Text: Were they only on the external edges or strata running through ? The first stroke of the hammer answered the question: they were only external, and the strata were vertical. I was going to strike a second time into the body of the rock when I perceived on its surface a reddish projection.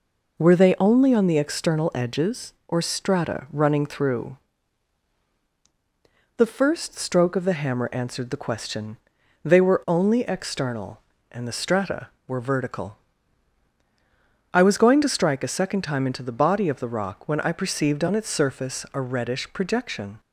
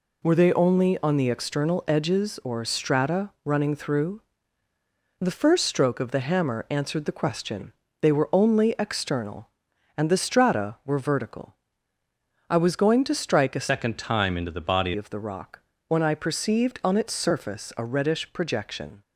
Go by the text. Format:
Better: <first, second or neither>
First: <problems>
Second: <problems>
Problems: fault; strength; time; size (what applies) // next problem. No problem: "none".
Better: first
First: none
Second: changes voice from "second" to "body"; from 13.6 to 14.9 s; 1.3 s long // pauses between "rock" and "when"; slight; at 15.5 s; 0.28 s long